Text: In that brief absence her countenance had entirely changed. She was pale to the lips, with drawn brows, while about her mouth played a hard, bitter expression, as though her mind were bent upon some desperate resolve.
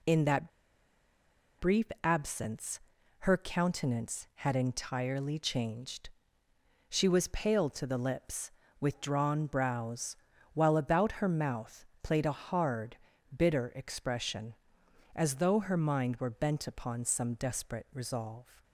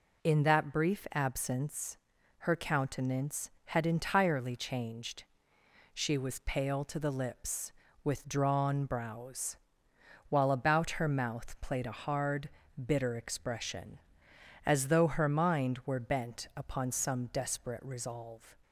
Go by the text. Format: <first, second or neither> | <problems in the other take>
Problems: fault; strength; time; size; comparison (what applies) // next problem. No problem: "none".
second | pauses between "that" and "brief"; at 0.4 s; 1.0 s long // pauses between "brief" and "absence"; slight; at 1.8 s; 0.18 s long // pauses between "absence" and "her"; noticeable; at 2.7 s; 0.46 s long; noticeable in the second // pauses between "mouth" and "played"; slight; at 11.8 s; 0.16 s long